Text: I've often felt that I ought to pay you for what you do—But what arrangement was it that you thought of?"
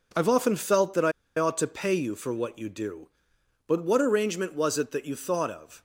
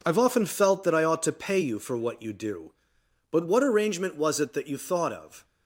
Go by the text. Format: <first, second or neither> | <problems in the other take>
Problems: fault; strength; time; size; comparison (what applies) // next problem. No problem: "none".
second | pauses between "I" and "ought"; slight; at 1.1 s; 0.27 s long